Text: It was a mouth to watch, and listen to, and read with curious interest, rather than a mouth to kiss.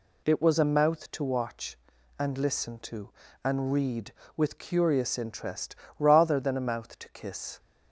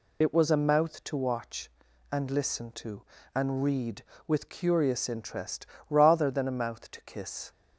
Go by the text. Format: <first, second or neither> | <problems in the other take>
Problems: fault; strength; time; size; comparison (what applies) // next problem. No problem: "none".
first | loses the start of "It"; at 0.2 s; 40 ms